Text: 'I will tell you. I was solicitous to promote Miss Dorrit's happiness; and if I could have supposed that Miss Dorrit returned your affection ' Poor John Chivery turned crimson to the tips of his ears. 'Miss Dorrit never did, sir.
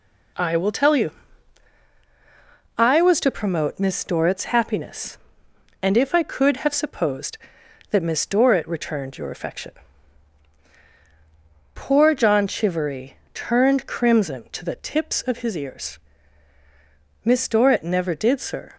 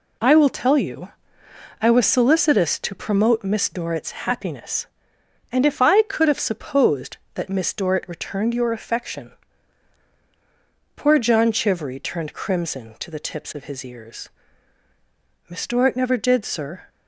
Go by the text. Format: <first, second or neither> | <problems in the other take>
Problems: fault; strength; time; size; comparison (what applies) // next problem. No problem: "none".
second | skips "solicitous"; at 3.2 s // pauses between "Chivery" and "turned"; slight; at 13.1 s; 0.18 s long